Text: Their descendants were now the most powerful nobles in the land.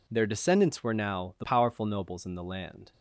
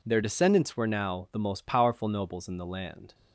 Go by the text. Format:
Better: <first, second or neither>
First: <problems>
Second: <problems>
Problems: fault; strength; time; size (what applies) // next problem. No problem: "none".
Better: second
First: skips "most"; at 1.4 s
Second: none